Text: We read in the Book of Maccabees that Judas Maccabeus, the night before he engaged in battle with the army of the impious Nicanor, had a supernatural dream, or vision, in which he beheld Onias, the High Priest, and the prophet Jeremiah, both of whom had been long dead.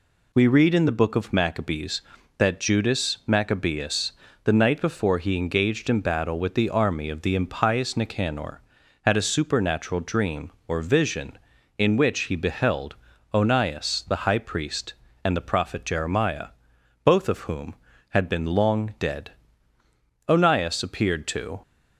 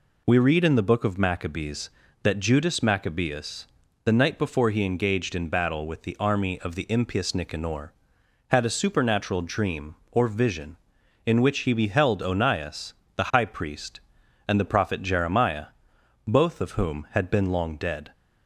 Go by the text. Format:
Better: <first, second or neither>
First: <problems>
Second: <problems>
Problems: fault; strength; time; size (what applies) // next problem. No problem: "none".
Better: second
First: pauses between "beheld" and "Onias"; at 12.9 s; 0.38 s long // goes on to say "Onias appeared to"; from 20.2 s on; 1.3 s long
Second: none